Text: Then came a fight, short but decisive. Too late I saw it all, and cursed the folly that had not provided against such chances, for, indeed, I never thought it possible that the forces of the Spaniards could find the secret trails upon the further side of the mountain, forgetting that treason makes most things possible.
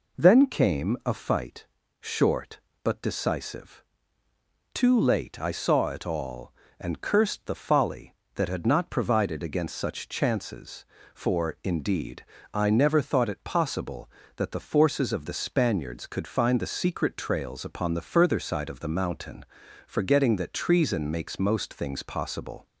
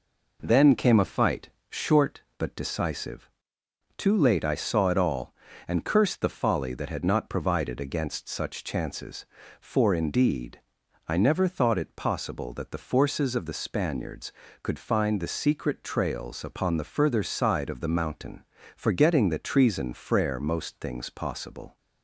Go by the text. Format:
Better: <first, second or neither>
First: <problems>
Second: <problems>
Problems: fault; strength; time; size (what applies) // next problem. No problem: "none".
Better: first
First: none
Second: says "frere" for "makes"; at 19.9 s